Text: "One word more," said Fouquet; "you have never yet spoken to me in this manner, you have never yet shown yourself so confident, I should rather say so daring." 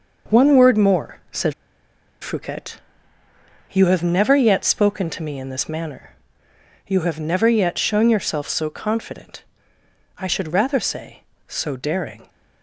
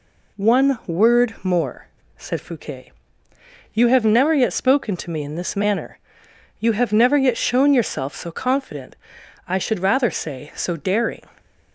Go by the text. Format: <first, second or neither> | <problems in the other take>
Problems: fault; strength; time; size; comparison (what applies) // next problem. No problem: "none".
second | pauses between "said" and "Fouquet"; noticeable; at 1.5 s; 0.68 s long